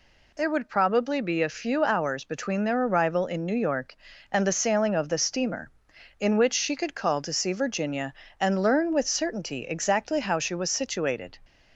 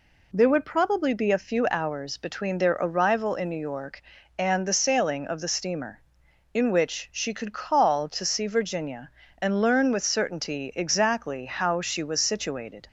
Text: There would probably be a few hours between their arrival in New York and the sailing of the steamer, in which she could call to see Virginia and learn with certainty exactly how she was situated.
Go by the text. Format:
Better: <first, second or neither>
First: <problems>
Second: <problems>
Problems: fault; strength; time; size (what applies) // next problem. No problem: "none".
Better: neither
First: none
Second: none